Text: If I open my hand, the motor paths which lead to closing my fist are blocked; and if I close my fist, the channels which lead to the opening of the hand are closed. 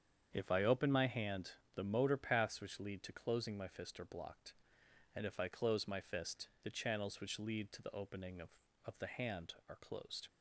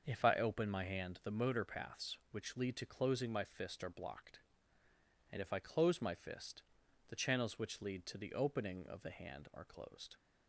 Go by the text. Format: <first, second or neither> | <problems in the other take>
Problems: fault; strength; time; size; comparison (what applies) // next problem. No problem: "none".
second | starts louder than the rest; strong; until 1.3 s; 8 dB; also in the second // says "of" twice; at 8.8 s